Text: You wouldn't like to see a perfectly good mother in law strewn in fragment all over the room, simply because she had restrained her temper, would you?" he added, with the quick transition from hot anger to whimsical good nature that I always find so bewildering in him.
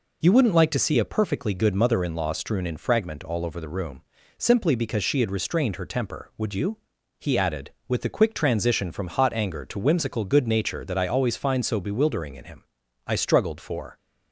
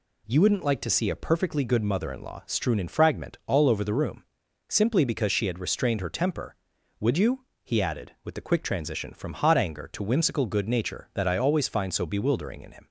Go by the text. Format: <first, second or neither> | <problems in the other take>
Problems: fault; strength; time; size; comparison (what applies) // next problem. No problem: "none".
second | goes on to say "I struggled for"; noticeable; from 13.0 s on; 0.90 s long